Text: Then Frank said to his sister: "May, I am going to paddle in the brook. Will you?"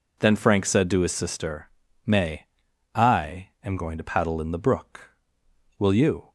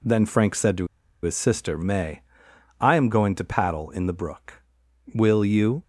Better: first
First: none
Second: pauses between "to" and "his"; at 0.8 s; 0.36 s long

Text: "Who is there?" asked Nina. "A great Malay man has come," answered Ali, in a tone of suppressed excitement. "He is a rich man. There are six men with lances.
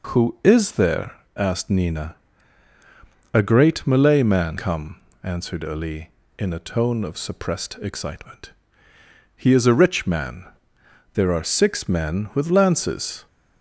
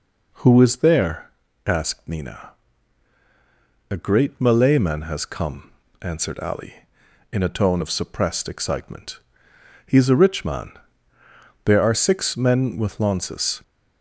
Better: second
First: skips "has"; at 4.5 s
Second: none

